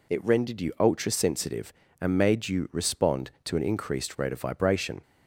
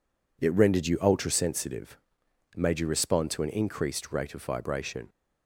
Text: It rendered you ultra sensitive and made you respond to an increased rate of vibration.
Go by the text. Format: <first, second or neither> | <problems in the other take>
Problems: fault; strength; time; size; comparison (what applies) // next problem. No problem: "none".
first | skips "and"; at 2.2 s